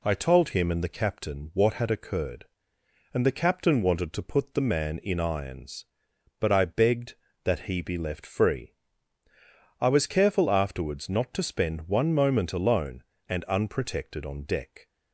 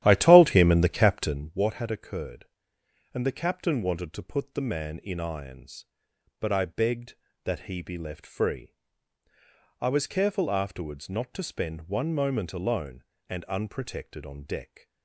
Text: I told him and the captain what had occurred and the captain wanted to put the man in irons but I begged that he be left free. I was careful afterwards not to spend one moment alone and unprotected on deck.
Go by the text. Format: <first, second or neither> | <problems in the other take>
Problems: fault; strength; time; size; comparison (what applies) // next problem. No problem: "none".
first | starts louder than the rest; strong; until 1.6 s; 12 dB